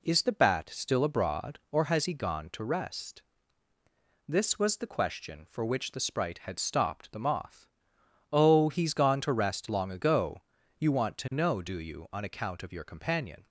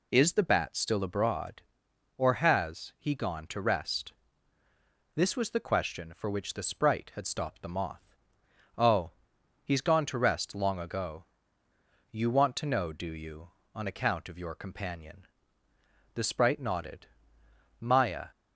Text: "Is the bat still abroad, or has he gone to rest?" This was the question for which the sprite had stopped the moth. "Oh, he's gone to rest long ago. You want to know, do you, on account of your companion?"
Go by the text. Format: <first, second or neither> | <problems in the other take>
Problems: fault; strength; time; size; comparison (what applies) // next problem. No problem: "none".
first | goes on to say "The sprite nodded Maya"; strong; from 16.1 s on; 2.1 s long